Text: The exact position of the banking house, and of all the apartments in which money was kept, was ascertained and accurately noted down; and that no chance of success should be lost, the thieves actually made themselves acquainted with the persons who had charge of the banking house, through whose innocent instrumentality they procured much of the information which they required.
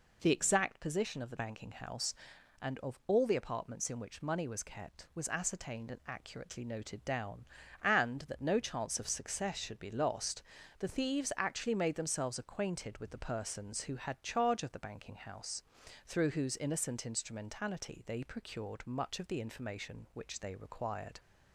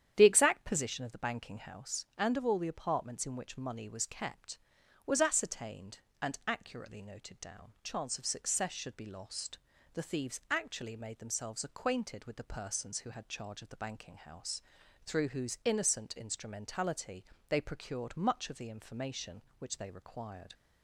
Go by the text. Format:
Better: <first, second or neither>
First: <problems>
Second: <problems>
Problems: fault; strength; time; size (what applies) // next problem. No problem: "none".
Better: first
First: none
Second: starts louder than the rest; strong; until 1.1 s; 9.5 dB // skips "and that no"; at 7.7 s // pauses between "instrumentality" and "they"; slight; at 17.2 s; 0.24 s long